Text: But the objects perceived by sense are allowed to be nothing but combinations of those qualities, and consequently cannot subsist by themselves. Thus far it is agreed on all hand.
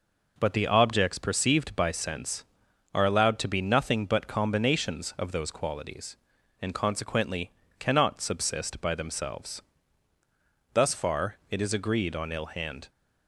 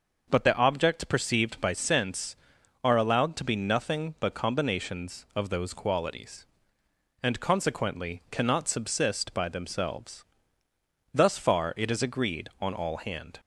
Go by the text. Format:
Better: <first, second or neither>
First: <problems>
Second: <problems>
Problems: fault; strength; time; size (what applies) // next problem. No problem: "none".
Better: second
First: pauses between "consequently" and "cannot"; slight; at 7.5 s; 0.28 s long // says "ill" for "all"; at 12.3 s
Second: none